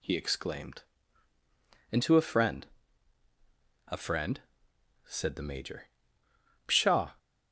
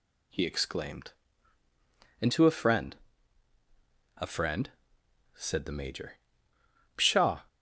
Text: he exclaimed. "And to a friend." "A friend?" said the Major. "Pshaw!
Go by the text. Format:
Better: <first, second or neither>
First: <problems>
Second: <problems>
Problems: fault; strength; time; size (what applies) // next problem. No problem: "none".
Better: neither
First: none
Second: none